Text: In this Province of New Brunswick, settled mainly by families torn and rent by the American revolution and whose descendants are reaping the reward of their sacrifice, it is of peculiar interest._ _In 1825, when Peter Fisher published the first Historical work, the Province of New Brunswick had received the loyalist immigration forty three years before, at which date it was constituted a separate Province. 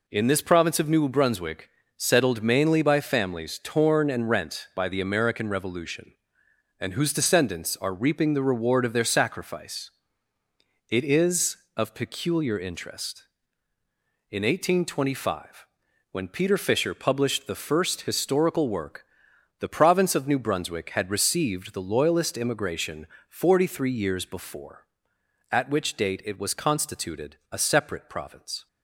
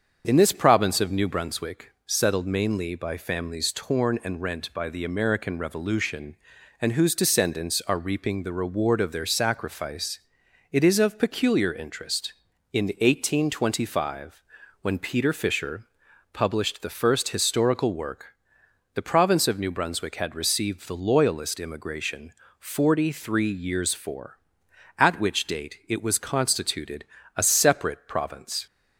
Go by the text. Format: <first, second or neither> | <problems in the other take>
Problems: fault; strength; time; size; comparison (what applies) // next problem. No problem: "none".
first | starts louder than the rest; strong; until 1.2 s; 7 dB // pauses between "Fisher" and "published"; noticeable; at 15.8 s; 0.46 s long // pauses between "immigration" and "forty"; slight; at 22.3 s; 0.26 s long; slight in the first // says "for" for "before"; at 23.9 s // pauses between "constituted" and "a"; slight; at 27.0 s; 0.32 s long; slight in the first